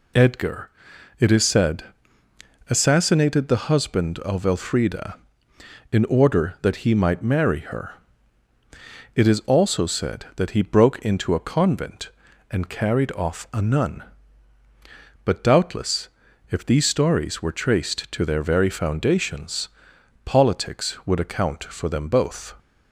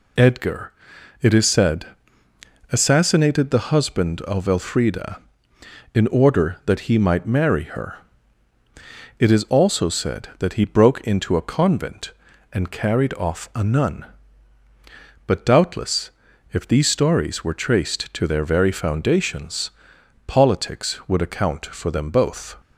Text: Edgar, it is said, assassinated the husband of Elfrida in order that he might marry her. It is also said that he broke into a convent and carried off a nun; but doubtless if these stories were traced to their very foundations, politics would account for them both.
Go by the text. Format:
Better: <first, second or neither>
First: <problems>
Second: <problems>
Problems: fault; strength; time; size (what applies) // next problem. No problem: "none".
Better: neither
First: pauses between "doubtless" and "if"; at 16.0 s; 0.40 s long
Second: pauses between "doubtless" and "if"; at 16.1 s; 0.40 s long